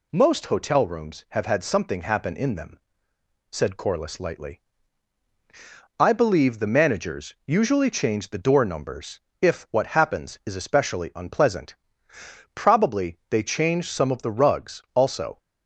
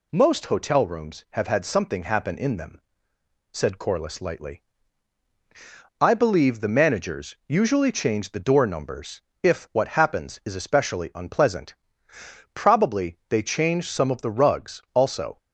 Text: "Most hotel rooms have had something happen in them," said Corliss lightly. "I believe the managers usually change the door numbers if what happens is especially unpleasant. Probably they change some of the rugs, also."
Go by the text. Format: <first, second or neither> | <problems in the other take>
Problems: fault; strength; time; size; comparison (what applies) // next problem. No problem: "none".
neither | pauses between "numbers" and "if"; slight; the same in both